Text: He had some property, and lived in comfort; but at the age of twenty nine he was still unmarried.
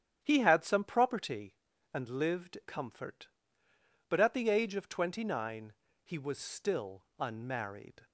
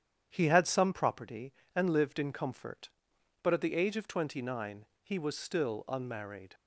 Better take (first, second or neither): second